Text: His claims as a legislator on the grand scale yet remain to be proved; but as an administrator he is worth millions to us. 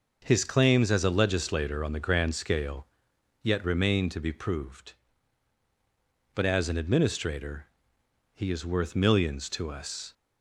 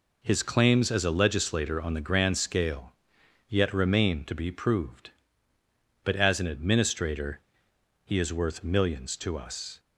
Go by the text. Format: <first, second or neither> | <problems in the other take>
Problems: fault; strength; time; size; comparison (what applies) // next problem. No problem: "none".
neither | pauses between "scale" and "yet"; noticeable; the same in both // pauses between "administrator" and "he"; noticeable; the same in both